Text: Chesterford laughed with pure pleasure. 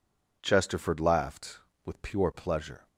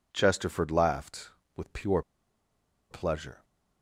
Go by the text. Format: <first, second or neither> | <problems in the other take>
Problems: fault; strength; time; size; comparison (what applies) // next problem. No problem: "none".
first | pauses between "pure" and "pleasure"; noticeable; at 2.0 s; 0.89 s long